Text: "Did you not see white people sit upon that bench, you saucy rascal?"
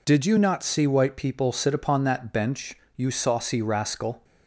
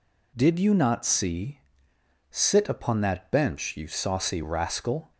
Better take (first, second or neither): first